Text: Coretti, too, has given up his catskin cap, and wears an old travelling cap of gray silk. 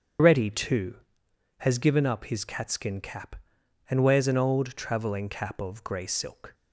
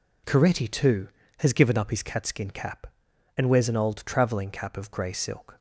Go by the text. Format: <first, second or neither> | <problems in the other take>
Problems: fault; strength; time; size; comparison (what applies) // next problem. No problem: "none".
second | loses the start of "Coretti"; at 0.1 s; 160 ms // starts louder than the rest; strong; until 1.8 s; 7 dB